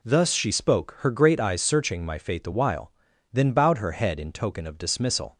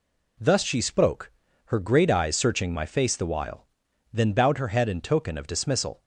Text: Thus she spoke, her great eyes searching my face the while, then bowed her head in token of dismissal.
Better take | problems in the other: second | says "fate" for "face"; at 2.1 s

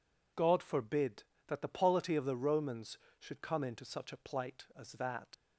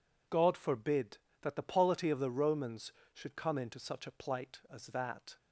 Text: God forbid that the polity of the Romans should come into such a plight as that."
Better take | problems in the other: second | leaves "that" unfinished; at 5.3 s; 85 ms

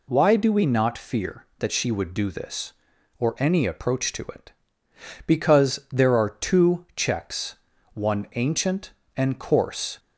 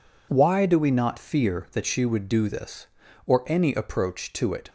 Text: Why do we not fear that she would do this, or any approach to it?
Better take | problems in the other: second | goes on to say "Because there are two checks one ancient and coarse"; strong; from 5.2 s on; 4.7 s long

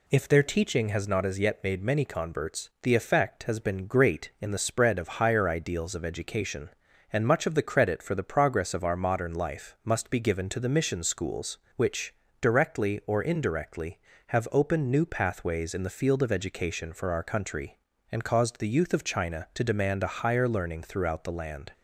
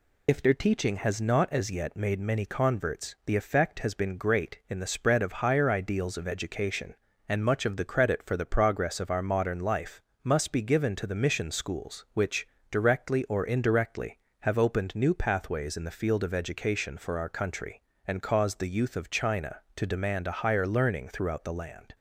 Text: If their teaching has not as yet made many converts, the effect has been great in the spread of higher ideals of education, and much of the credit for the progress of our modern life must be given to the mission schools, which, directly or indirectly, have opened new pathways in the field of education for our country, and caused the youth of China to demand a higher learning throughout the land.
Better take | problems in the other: first | loses the start of "If"; at 0.2 s; 35 ms // pauses between "life" and "must"; slight; at 10.0 s; 0.24 s long

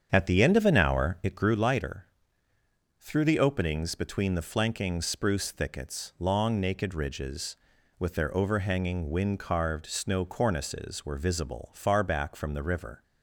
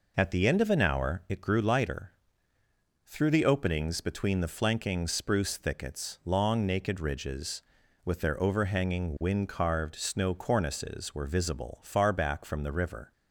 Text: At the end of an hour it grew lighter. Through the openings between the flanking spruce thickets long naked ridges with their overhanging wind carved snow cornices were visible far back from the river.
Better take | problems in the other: second | starts louder than the rest; strong; until 1.6 s; 8 dB

